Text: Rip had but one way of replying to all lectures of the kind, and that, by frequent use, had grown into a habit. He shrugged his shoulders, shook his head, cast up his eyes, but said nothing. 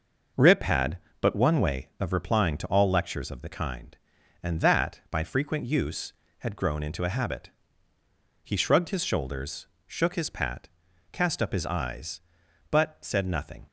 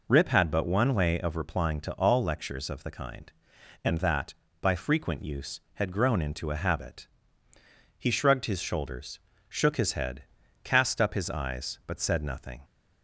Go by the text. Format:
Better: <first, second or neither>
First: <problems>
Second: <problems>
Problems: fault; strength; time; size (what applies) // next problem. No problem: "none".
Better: second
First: says "pat" for "head"; at 10.2 s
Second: none